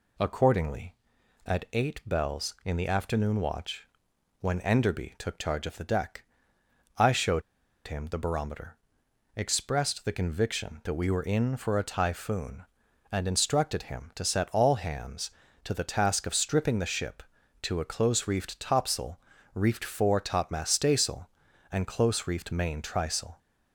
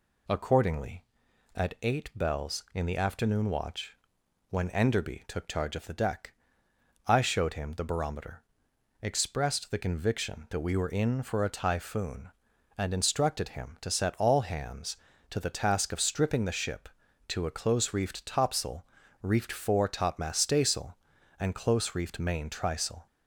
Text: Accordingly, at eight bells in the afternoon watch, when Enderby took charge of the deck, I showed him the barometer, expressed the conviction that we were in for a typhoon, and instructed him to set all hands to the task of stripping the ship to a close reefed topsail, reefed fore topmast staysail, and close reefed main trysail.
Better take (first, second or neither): second